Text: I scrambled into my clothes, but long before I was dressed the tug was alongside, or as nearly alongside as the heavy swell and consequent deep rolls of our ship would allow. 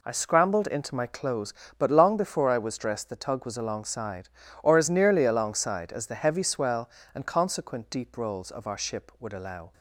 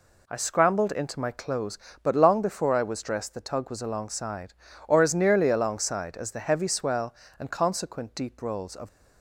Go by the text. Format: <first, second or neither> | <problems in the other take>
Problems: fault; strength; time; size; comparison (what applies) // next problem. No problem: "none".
first | stops before "our ship would allow"; at 8.8 s